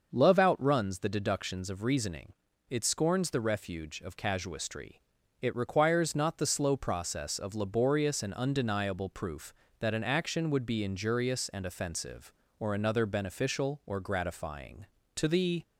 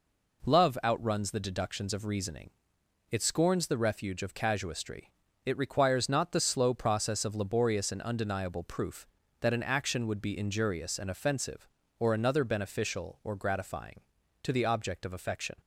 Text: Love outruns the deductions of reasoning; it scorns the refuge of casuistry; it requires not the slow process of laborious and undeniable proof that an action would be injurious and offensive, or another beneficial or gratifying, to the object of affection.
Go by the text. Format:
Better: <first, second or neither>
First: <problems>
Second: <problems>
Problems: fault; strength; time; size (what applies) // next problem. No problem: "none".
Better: second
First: starts louder than the rest; noticeable; until 1.1 s; 6 dB // stops before "object of affection"; at 15.6 s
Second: none